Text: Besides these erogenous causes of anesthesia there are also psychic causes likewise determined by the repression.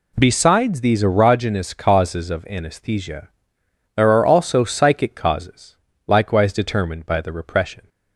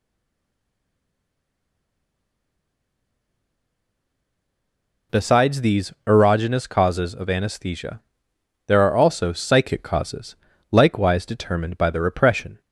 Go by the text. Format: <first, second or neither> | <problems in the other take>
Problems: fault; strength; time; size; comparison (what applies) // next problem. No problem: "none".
first | stays silent before the first word; strong; until 5.1 s; 5.1 s long // pauses between "anesthesia" and "there"; noticeable; at 8.0 s; 0.66 s long; noticeable in the first // pauses between "causes" and "likewise"; slight; at 10.3 s; 0.34 s long; slight in the first